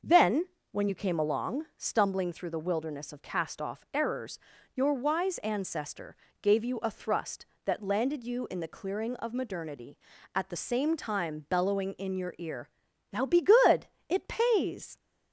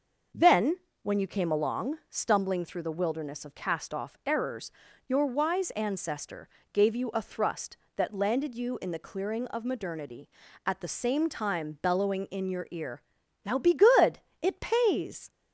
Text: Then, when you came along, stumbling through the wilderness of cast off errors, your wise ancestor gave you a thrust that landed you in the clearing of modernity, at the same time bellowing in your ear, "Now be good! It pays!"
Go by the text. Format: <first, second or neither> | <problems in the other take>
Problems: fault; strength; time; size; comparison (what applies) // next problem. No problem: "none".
neither | starts louder than the rest; the same in both // pauses between "ancestor" and "gave"; slight; the same in both